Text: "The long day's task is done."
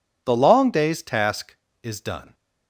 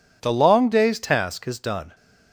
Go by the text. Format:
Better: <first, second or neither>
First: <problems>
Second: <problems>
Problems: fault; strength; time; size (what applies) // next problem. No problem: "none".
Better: neither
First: none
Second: none